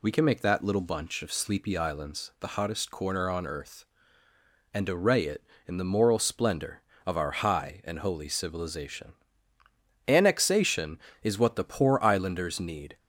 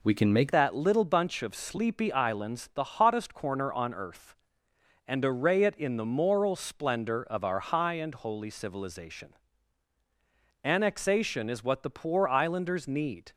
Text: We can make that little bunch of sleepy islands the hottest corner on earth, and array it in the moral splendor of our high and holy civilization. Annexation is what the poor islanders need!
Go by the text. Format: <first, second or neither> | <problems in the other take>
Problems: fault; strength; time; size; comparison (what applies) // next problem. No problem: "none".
first | changes voice at "that"; from 0.5 s on; 12.8 s long